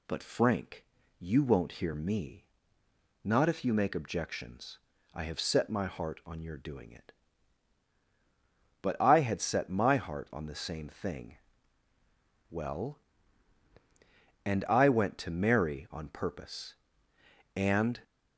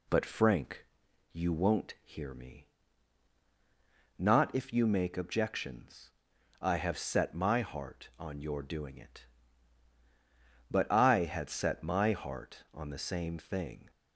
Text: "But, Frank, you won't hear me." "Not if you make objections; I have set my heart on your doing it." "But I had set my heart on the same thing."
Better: second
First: goes on to say "Well And I went to Mary on purpose and"; strong; from 12.5 s on; 5.5 s long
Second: none

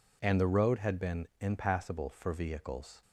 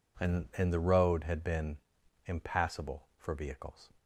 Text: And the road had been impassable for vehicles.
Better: first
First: none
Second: says "And" twice; at 0.5 s // pauses between "been" and "impassable"; noticeable; at 1.7 s; 0.48 s long

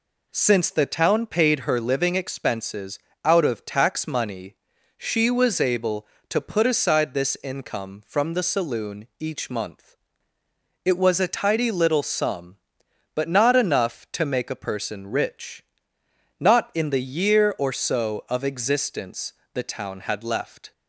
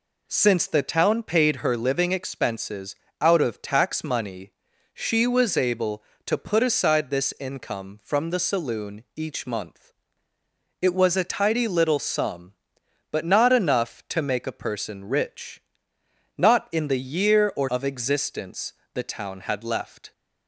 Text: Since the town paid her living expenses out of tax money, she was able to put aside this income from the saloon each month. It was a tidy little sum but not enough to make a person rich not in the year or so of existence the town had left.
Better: first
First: pauses between "expenses" and "out"; slight; at 2.9 s; 0.26 s long // pauses between "rich" and "not"; noticeable; at 15.6 s; 0.74 s long // pauses between "existence" and "the"; slight; at 19.3 s; 0.22 s long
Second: pauses between "expenses" and "out"; slight; at 2.9 s; 0.26 s long // pauses between "rich" and "not"; noticeable; at 15.6 s; 0.74 s long // skips "so"; at 17.6 s // pauses between "existence" and "the"; slight; at 18.7 s; 0.22 s long

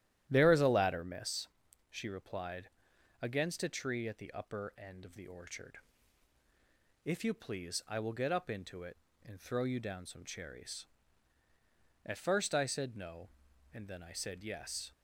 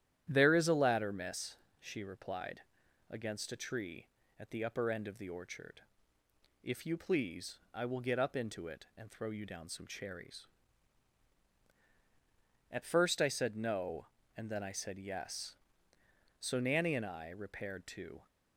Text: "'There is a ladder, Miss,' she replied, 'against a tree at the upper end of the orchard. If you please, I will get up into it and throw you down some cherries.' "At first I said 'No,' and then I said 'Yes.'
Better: first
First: starts louder than the rest; strong; until 1.3 s; 12 dB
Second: starts louder than the rest; strong; until 1.3 s; 11 dB // goes on to say "So Nanny and I repaired to"; strong; from 16.4 s on; 1.8 s long

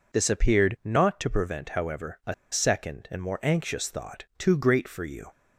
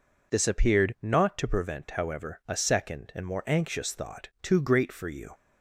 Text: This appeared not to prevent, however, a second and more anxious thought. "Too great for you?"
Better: second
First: pauses between "a" and "second"; slight; at 2.3 s; 0.17 s long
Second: none

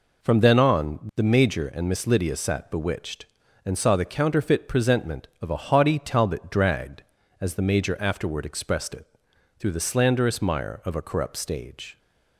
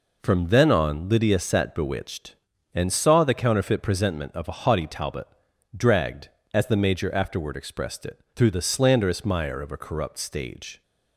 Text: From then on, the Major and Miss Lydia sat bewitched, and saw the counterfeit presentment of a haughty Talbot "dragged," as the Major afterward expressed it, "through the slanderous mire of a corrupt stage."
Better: first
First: none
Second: skips "the Major and Miss"; at 1.0 s // pauses between "Talbot" and "dragged"; noticeable; at 5.2 s; 0.48 s long

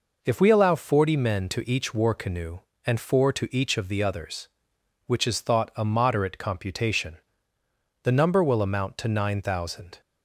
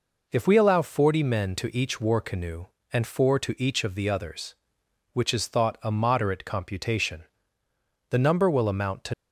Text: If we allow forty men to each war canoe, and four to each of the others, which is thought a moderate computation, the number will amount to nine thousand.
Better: first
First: none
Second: stops before "nine thousand"; at 9.1 s

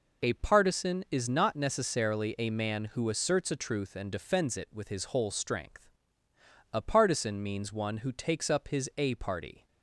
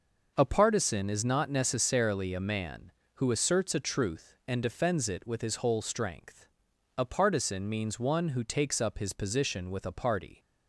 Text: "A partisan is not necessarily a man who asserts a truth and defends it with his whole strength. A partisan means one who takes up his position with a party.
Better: second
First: skips "position with"; at 8.9 s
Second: none

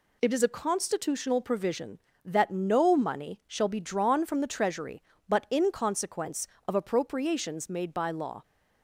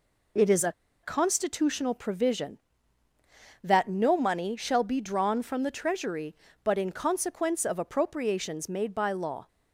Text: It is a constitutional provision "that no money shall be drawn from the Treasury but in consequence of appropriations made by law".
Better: first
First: none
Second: pauses between "a" and "constitutional"; slight; at 0.7 s; 0.30 s long

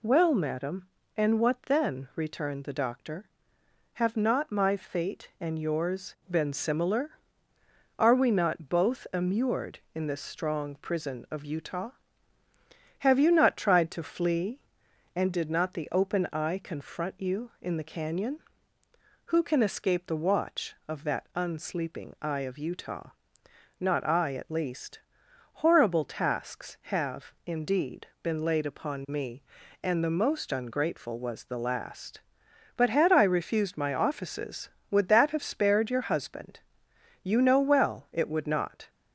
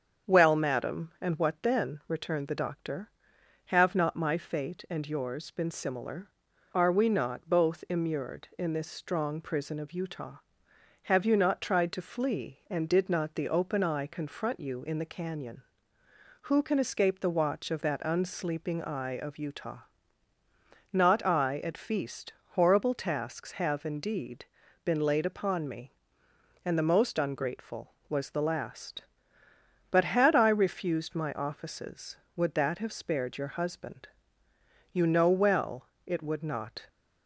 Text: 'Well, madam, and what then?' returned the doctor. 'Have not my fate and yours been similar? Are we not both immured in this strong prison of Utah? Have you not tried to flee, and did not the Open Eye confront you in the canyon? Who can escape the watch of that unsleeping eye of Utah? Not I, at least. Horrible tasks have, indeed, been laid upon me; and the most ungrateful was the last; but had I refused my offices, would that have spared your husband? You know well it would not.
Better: first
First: none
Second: starts louder than the rest; strong; until 1.3 s; 7.5 dB // says "feast" for "least"; at 21.7 s // pauses between "well" and "it"; slight; at 35.8 s; 0.18 s long

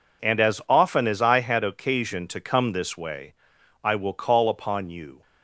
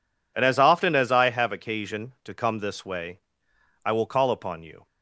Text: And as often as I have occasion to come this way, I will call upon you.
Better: second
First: says "had" for "have"; at 1.3 s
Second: none

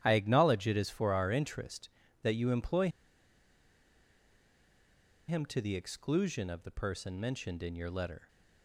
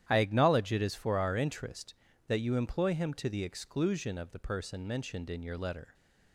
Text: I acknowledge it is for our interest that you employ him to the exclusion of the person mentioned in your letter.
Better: second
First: starts louder than the rest; strong; until 1.0 s; 11 dB // pauses between "employ" and "him"; strong; at 2.8 s; 2.3 s long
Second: starts louder than the rest; strong; until 1.1 s; 11 dB

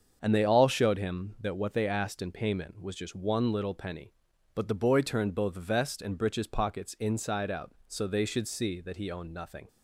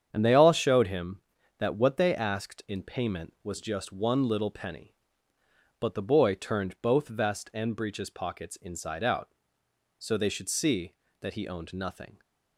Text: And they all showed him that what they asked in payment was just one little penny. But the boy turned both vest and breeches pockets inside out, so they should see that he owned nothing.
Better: neither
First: starts louder than the rest; until 1.2 s; 7 dB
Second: starts louder than the rest; strong; until 1.1 s; 8 dB

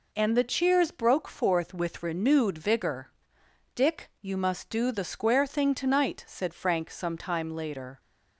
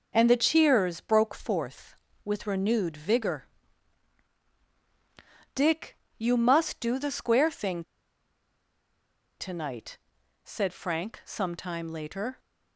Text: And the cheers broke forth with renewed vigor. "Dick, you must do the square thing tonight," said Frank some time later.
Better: first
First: none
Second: pauses between "thing" and "tonight"; strong; at 7.8 s; 1.5 s long

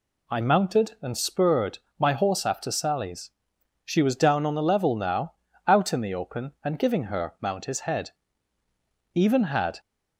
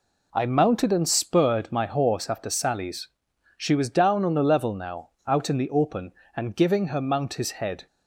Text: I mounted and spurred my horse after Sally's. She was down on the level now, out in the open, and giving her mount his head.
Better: second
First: pauses between "spurred" and "my"; slight; at 1.7 s; 0.20 s long // goes on to say "Even had"; noticeable; from 9.1 s on; 0.64 s long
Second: none

